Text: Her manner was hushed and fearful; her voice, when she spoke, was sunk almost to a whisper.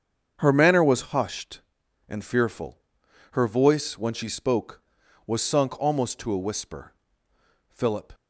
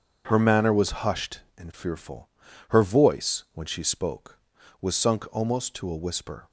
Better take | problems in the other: second | starts louder than the rest; strong; until 1.3 s; 7 dB; also in the second // goes on to say "Philip"; slight; from 7.6 s on; 0.44 s long

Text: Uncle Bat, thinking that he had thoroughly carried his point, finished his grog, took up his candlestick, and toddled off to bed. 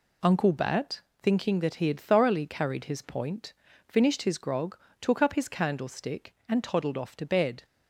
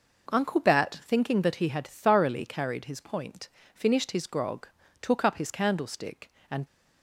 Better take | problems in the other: first | stops before "toddled off to bed"; at 6.6 s

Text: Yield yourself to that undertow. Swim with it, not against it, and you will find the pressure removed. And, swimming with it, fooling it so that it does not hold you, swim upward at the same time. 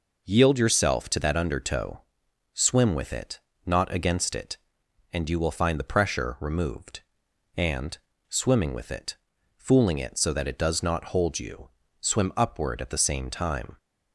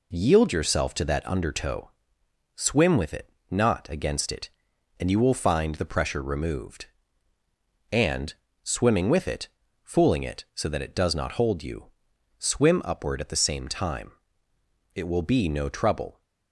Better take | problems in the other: first | goes on to say "It will be no trouble"; noticeable; from 14.9 s on; 1.2 s long

